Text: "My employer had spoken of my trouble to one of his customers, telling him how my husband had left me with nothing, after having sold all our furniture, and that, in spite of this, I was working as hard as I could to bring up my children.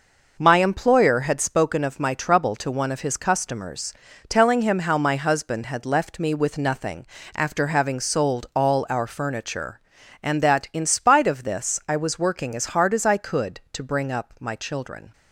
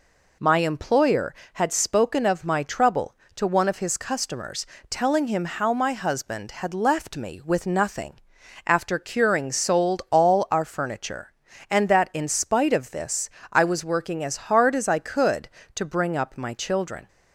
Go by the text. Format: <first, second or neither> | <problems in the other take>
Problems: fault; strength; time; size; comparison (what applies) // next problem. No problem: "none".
first | says "curing" for "having"; at 8.9 s